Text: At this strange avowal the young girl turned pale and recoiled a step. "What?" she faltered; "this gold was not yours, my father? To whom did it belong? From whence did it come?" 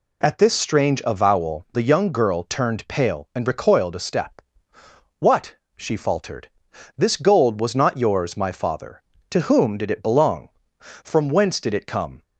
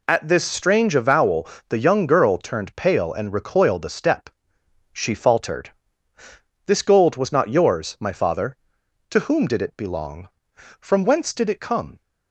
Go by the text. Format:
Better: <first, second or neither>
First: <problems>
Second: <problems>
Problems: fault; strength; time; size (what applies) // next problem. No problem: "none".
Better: first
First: none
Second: pauses between "avowal" and "the"; slight; at 1.4 s; 0.22 s long // skips "What"; at 4.5 s